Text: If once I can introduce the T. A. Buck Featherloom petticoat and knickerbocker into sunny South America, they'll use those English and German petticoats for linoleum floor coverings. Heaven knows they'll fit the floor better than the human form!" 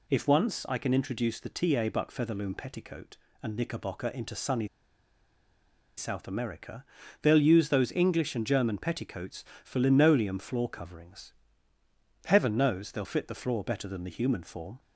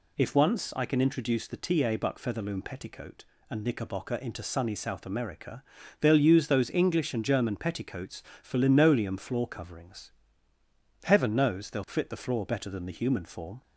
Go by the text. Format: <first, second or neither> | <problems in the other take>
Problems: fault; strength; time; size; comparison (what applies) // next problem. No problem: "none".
second | pauses between "sunny" and "South"; strong; at 4.6 s; 1.2 s long